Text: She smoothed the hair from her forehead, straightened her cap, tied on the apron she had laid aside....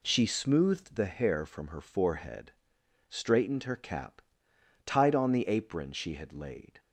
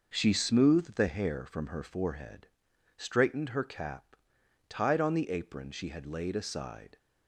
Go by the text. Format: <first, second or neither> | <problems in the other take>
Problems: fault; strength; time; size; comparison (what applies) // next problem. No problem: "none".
second | stops before "aside"; at 6.7 s